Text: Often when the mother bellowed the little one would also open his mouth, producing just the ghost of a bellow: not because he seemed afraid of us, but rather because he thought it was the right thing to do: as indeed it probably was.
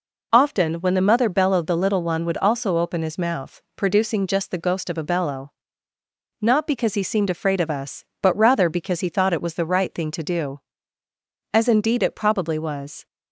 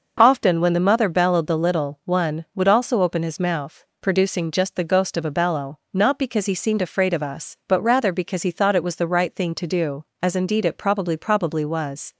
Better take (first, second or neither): first